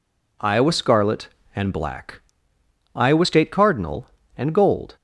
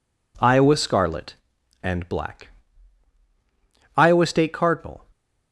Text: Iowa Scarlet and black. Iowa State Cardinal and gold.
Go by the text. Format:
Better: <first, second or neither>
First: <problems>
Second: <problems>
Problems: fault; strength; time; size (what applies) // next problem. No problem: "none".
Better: first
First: none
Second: stops before "and gold"; at 5.1 s